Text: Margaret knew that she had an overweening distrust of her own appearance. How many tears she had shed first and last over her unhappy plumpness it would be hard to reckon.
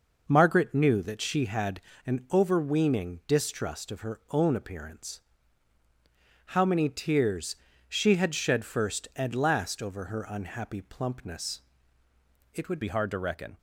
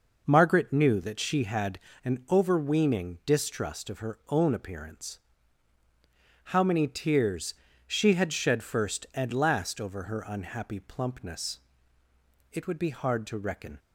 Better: second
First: pauses between "had" and "an"; slight; at 1.7 s; 0.24 s long // pauses between "tears" and "she"; slight; at 7.5 s; 0.34 s long // pauses between "plumpness" and "it"; noticeable; at 11.5 s; 0.94 s long // changes voice at "be"; from 12.8 s on; 0.7 s long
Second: pauses between "had" and "an"; slight; at 1.7 s; 0.24 s long // pauses between "tears" and "she"; slight; at 7.5 s; 0.34 s long // pauses between "plumpness" and "it"; noticeable; at 11.5 s; 0.94 s long

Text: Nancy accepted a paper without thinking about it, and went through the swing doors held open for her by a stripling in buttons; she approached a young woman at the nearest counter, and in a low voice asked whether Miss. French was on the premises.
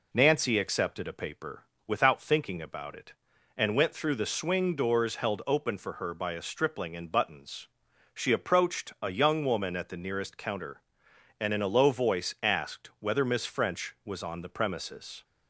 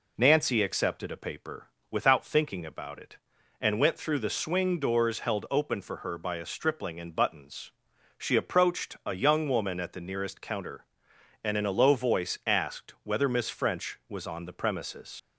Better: first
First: pauses between "paper" and "without"; slight; at 1.6 s; 0.20 s long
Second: pauses between "paper" and "without"; slight; at 1.6 s; 0.20 s long // leaves "premises" unfinished; at 15.1 s; 75 ms

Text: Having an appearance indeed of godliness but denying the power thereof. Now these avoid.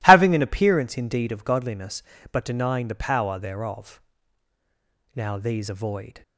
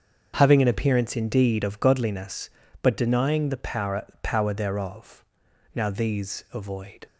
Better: first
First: none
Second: starts louder than the rest; until 1.3 s; 6.5 dB // says "power" twice; at 4.2 s

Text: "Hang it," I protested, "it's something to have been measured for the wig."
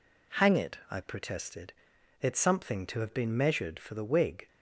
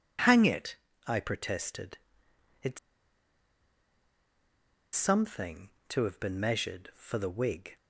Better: first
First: none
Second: pauses between "it's" and "something"; strong; at 2.7 s; 2.1 s long

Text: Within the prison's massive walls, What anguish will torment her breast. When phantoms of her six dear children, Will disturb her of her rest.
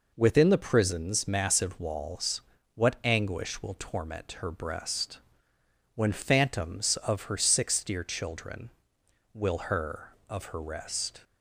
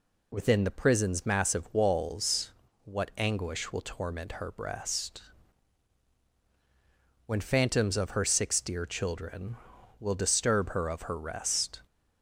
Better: second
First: skips "disturb"; at 9.5 s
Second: none

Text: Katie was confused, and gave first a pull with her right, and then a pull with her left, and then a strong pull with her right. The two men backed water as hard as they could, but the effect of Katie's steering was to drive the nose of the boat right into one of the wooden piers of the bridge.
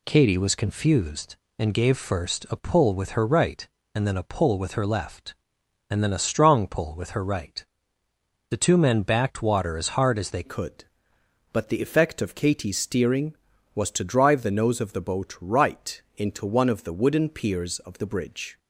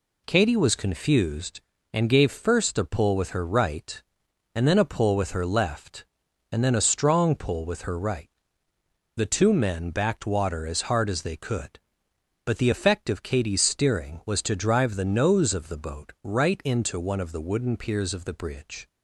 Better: second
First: changes voice at "could"; from 10.4 s on; 8.1 s long // pauses between "right" and "into"; slight; at 15.9 s; 0.16 s long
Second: none

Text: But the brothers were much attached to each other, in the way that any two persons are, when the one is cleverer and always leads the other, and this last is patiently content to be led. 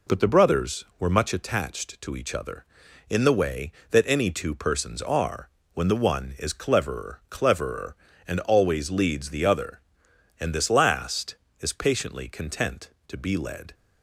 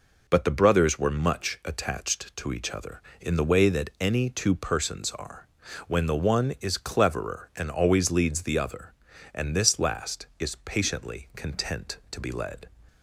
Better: second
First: says "cleverer" twice; at 7.2 s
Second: none

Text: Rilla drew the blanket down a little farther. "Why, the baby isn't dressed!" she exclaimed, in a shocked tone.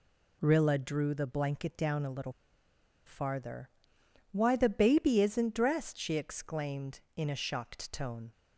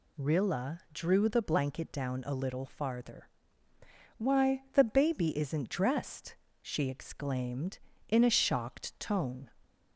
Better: second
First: pauses between "little" and "farther"; noticeable; at 2.3 s; 0.74 s long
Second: none

